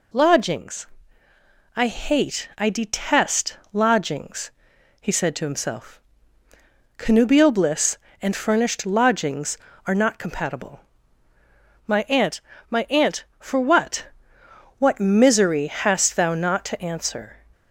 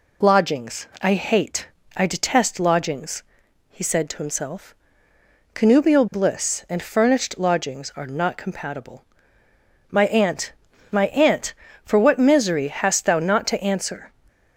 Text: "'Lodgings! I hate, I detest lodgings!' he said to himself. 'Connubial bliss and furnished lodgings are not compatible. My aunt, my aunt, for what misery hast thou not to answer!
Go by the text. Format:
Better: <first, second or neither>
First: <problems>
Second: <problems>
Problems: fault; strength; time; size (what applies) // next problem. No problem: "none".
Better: second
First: pauses between "detest" and "lodgings"; slight; at 3.5 s; 0.16 s long // says "what" twice; at 14.7 s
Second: none